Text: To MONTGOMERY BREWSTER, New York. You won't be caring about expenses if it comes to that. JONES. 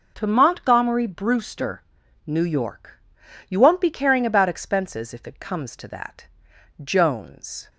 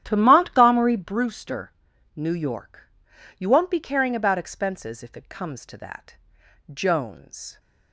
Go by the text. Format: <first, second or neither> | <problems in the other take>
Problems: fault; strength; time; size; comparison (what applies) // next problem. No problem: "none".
first | starts louder than the rest; strong; until 1.3 s; 11 dB